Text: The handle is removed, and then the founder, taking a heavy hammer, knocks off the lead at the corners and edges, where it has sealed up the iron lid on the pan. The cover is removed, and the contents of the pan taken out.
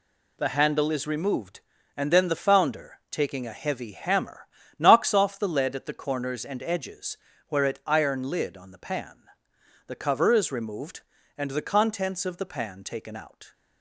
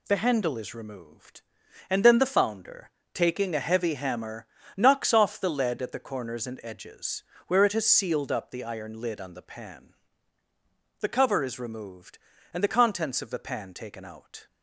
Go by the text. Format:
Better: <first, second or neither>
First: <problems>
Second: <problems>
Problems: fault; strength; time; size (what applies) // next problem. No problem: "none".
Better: second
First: skips "has sealed up the"; at 7.8 s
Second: none